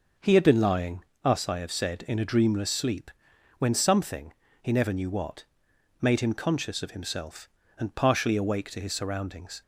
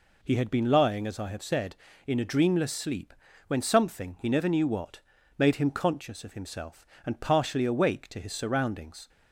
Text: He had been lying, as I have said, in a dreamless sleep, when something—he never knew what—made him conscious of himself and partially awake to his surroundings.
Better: second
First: says "us" for "as"; at 1.2 s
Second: none

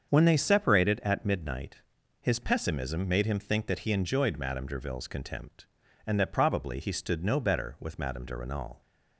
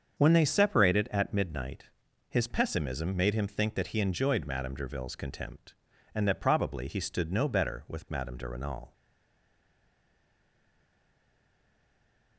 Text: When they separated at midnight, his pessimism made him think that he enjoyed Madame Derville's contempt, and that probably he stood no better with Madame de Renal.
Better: first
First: starts louder than the rest; strong; until 1.1 s; 7 dB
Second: starts louder than the rest; strong; until 1.2 s; 7 dB // stays silent after the last word; strong; from 8.9 s on; 3.4 s long

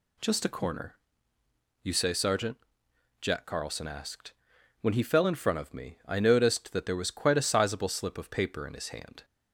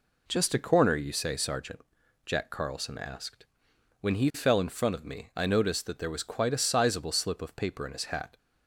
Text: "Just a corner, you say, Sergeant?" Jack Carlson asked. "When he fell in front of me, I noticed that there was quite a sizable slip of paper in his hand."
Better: first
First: none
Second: says "hat" for "hand"; at 8.0 s

